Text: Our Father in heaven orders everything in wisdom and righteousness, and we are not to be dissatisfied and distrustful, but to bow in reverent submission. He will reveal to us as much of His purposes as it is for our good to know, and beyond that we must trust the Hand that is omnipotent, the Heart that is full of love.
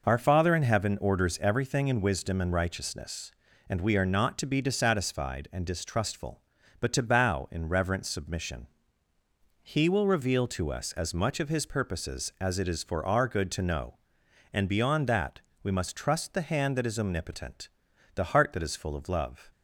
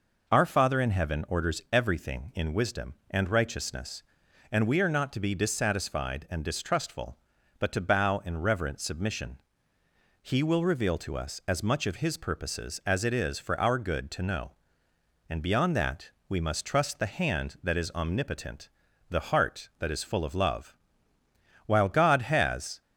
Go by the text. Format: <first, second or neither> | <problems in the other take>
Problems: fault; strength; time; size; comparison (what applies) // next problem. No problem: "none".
first | pauses between "that" and "we"; slight; at 16.1 s; 0.16 s long; slight in the first // goes on to say "While God has"; noticeable; from 21.6 s on; 1.1 s long